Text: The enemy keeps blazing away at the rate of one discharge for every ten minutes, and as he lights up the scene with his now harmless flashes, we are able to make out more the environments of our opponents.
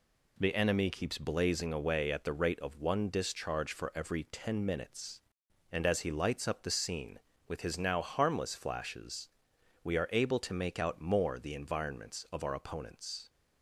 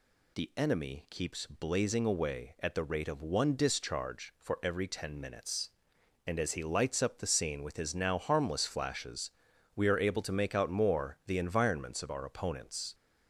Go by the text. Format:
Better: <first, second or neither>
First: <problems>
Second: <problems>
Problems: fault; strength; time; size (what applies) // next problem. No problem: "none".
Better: neither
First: none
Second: none